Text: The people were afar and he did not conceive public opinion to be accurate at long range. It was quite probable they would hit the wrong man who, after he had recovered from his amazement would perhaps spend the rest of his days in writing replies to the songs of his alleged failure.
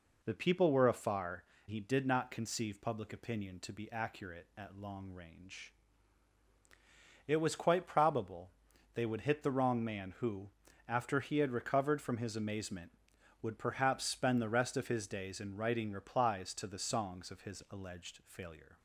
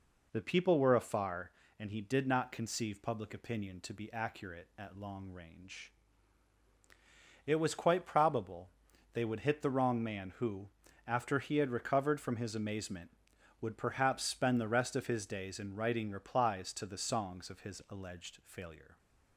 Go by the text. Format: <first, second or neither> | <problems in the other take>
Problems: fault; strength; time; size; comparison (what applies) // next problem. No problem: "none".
second | skips "and"; at 1.5 s // pauses between "probable" and "they"; at 8.5 s; 0.44 s long; also in the second